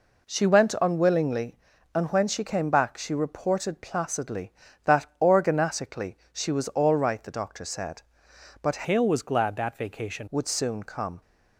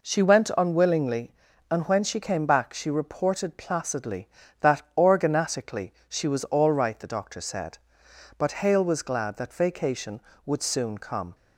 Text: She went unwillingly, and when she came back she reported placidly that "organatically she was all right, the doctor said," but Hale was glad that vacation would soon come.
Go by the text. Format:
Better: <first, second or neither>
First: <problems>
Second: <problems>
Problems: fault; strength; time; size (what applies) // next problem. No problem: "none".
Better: second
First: pauses between "that" and "organatically"; slight; at 5.0 s; 0.16 s long // pauses between "organatically" and "she"; slight; at 6.1 s; 0.16 s long // changes voice from "Hale" to "vacation"; from 8.8 to 10.2 s; 1.4 s long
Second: pauses between "that" and "organatically"; slight; at 4.8 s; 0.16 s long // pauses between "organatically" and "she"; slight; at 5.9 s; 0.16 s long